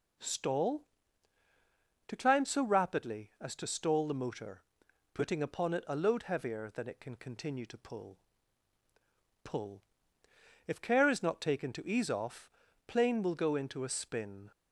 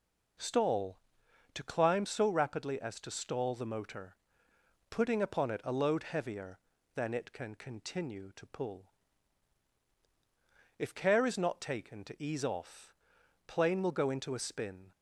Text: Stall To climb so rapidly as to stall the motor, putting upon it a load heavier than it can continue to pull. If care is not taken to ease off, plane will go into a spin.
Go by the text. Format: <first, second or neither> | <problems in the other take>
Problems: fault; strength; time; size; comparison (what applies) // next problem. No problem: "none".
second | says "pull" twice; at 9.4 s